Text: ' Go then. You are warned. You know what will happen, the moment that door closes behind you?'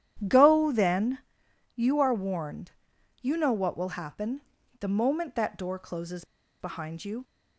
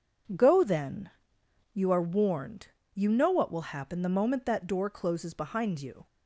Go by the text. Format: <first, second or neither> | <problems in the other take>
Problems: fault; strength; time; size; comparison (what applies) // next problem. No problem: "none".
second | starts louder than the rest; strong; until 1.2 s; 10.5 dB // pauses between "closes" and "behind"; at 6.2 s; 0.36 s long